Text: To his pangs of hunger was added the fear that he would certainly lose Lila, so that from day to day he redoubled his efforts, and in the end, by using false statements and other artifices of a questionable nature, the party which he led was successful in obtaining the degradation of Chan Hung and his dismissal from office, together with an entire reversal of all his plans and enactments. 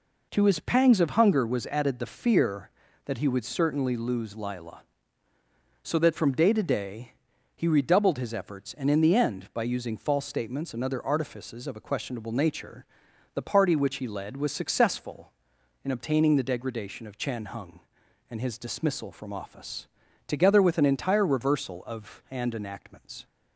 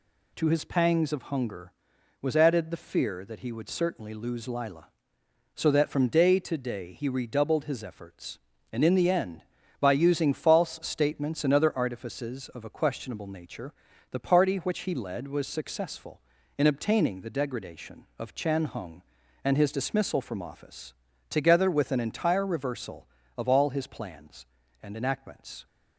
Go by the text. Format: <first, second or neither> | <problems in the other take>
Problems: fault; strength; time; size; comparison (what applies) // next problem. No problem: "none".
second | pauses between "day" and "he"; at 7.1 s; 0.42 s long // skips "all his plans"; at 22.2 s